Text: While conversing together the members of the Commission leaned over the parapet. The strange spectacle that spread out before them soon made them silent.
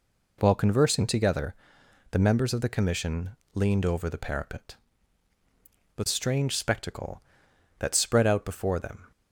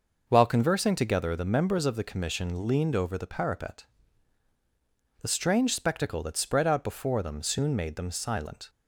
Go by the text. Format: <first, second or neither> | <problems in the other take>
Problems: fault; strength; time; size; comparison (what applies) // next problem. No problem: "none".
second | pauses between "together" and "the"; noticeable; at 1.5 s; 0.58 s long // pauses between "Commission" and "leaned"; slight; at 3.3 s; 0.22 s long // stops before "soon made them silent"; at 9.1 s